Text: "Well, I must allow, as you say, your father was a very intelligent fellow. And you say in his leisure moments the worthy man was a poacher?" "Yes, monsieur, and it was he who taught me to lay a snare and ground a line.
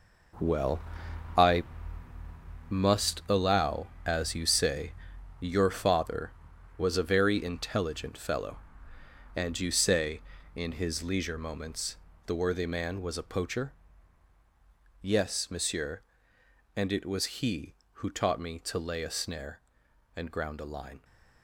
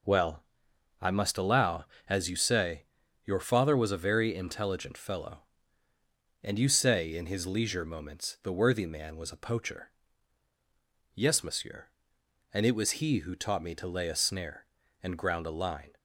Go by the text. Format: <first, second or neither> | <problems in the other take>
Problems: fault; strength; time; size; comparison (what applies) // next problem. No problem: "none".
second | gets quieter; strong; throughout; 11.5 dB // pauses between "I" and "must"; at 1.6 s; 1.0 s long // pauses between "moments" and "the"; slight; at 11.9 s; 0.30 s long